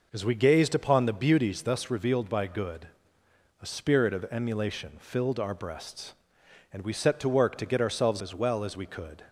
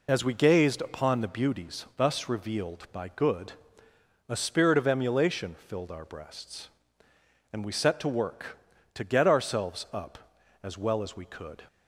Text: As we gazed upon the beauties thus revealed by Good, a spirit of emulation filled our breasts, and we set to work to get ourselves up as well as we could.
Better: second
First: skips "up"; at 8.2 s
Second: none

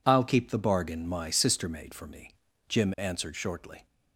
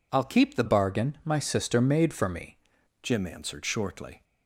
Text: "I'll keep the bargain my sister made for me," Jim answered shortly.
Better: first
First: none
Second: changes voice from "bargain" to "me"; from 0.6 to 2.5 s; 1.9 s long

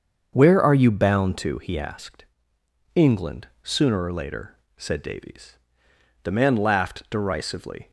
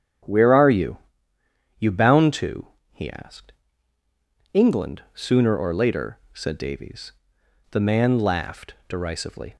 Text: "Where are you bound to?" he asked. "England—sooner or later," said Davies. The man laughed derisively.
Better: first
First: starts louder than the rest; until 1.3 s; 7 dB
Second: starts louder than the rest; strong; until 2.0 s; 9 dB // says "you" twice; at 1.7 s

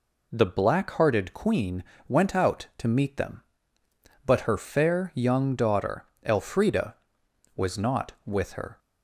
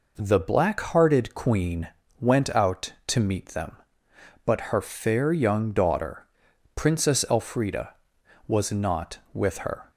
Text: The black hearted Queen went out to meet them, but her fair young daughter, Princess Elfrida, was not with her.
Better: second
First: pauses between "Queen" and "went"; slight; at 1.8 s; 0.24 s long // skips "Princess"; at 6.1 s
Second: pauses between "Queen" and "went"; slight; at 1.8 s; 0.32 s long

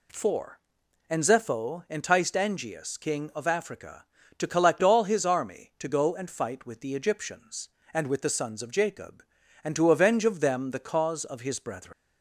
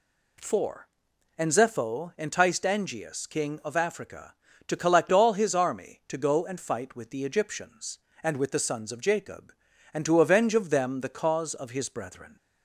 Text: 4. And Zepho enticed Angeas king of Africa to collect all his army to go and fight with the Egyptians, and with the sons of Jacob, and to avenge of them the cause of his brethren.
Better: second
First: leaves "brethren" unfinished; at 11.9 s; 135 ms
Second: none

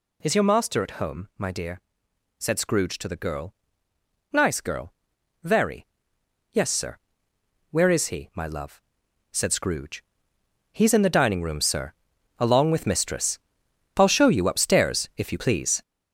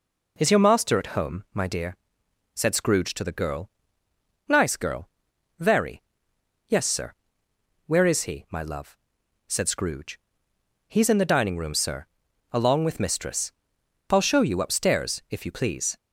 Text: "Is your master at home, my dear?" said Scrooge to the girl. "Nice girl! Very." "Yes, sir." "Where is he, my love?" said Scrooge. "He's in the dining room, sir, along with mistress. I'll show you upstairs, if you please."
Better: second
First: gets louder; strong; throughout; 7.5 dB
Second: none

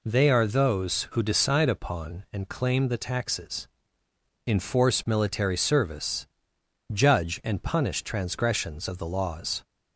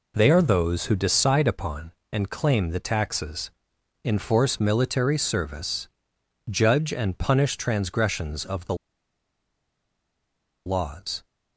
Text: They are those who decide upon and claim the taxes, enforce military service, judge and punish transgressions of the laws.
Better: first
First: none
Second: pauses between "the" and "laws"; strong; at 8.7 s; 1.9 s long

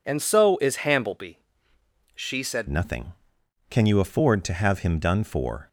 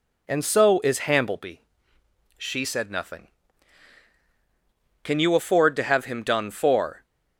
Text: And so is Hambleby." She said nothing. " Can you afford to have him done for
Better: second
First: changes voice at "nothing"; from 2.6 s on; 3.0 s long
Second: none

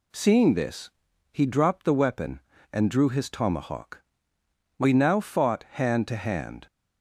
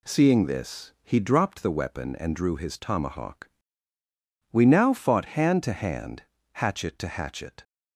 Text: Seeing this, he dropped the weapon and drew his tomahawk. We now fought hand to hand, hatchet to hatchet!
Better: second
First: stops before "hatchet to hatchet"; at 6.6 s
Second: none

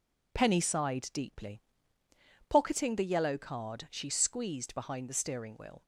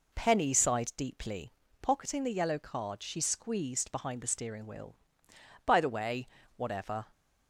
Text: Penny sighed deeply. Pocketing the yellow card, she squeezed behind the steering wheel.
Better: first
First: none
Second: goes on to say "By the way whatever"; from 5.6 s on; 1.4 s long

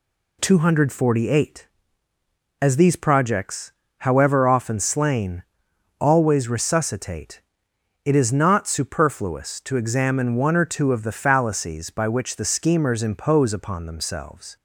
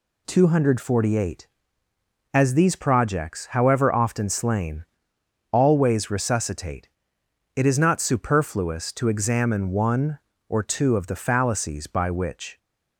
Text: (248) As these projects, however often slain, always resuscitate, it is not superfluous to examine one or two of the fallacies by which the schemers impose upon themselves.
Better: first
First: none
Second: stops before "the schemers impose upon themselves"; at 12.5 s

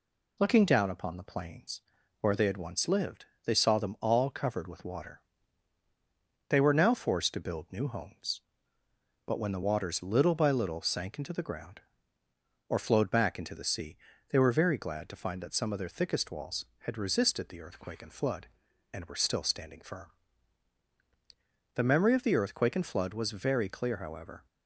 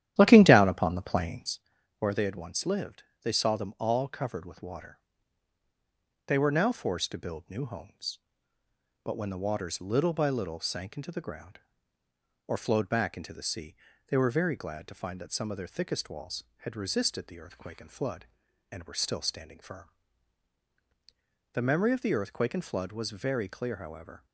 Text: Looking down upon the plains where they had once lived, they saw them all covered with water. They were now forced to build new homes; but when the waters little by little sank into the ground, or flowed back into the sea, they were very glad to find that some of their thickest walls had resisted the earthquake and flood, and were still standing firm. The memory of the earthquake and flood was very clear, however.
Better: first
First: pauses between "plains" and "where"; at 1.8 s; 0.38 s long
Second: starts louder than the rest; strong; until 1.7 s; 11.5 dB // pauses between "plains" and "where"; at 1.5 s; 0.38 s long

